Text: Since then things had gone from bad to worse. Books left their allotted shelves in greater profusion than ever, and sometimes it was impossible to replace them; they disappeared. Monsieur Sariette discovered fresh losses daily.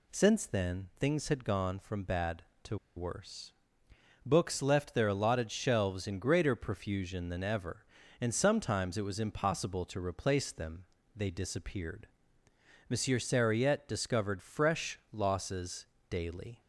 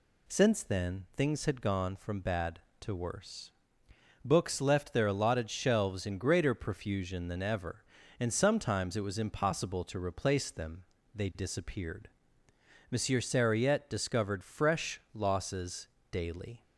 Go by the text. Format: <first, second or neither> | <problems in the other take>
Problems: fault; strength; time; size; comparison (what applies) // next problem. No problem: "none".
second | pauses between "to" and "worse"; slight; at 2.7 s; 0.19 s long // pauses between "losses" and "daily"; slight; at 15.8 s; 0.24 s long; slight in the second